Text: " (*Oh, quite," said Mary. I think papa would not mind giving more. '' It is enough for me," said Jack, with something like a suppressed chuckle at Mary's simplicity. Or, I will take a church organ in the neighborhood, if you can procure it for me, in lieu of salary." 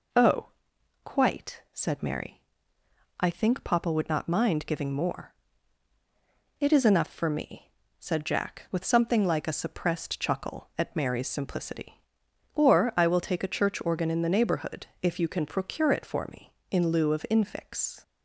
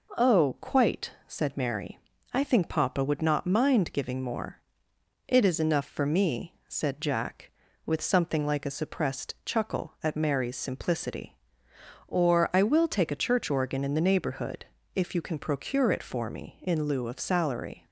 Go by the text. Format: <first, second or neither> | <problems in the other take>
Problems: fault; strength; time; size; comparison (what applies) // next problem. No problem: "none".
second | says "infix" for "salary"; at 17.3 s